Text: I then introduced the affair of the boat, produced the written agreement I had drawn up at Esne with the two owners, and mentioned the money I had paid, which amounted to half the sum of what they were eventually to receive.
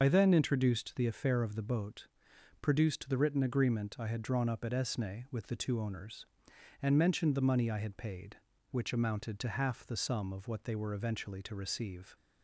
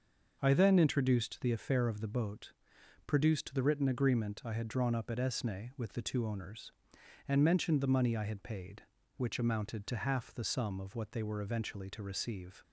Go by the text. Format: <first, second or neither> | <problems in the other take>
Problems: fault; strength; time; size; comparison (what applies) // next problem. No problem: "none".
second | loses the start of "I"; at 0.0 s; 50 ms // starts louder than the rest; noticeable; until 1.0 s; 6 dB; also in the second